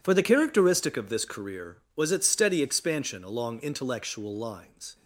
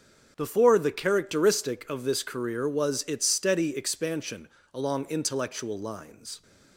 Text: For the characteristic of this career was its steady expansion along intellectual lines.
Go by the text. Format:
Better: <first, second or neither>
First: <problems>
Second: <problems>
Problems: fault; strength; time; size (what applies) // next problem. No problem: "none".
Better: first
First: none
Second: starts louder than the rest; until 1.3 s; 7 dB // says "Before" for "For"; at 0.3 s // pauses between "expansion" and "along"; slight; at 4.4 s; 0.24 s long